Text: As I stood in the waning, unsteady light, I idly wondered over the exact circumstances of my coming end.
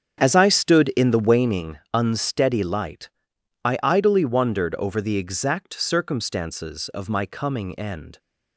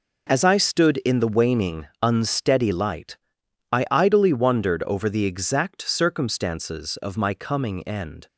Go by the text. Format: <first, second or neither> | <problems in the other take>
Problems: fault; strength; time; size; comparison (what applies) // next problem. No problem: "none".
second | starts louder than the rest; strong; until 1.5 s; 8 dB